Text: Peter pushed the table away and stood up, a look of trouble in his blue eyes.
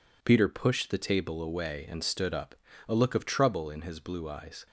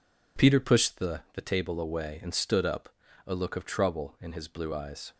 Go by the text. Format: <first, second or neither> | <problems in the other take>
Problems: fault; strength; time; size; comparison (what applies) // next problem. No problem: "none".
first | says "the" twice; at 1.3 s